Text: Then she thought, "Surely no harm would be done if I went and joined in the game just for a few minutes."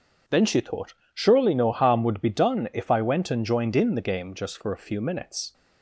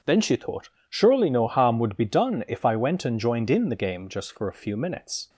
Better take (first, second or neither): neither